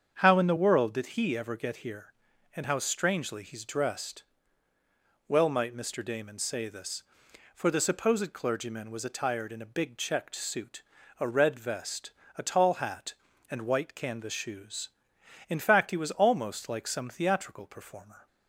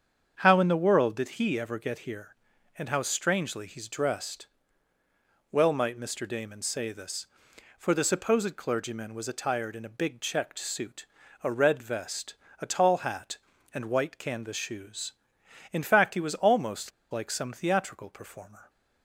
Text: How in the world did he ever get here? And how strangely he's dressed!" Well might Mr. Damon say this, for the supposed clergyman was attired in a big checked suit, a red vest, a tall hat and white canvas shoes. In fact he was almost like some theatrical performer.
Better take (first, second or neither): first